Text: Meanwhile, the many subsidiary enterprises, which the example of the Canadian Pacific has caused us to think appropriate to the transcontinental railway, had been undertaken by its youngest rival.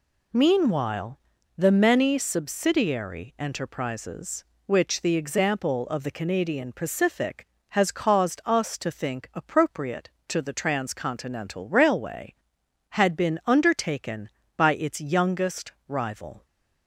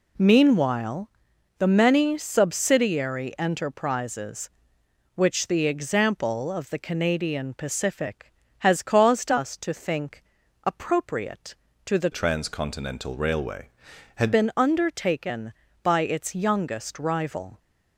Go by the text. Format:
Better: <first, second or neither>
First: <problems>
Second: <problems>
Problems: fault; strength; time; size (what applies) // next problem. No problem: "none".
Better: first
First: none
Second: pauses between "think" and "appropriate"; at 10.2 s; 0.42 s long // changes voice from "transcontinental" to "had"; from 12.1 to 14.3 s; 2.2 s long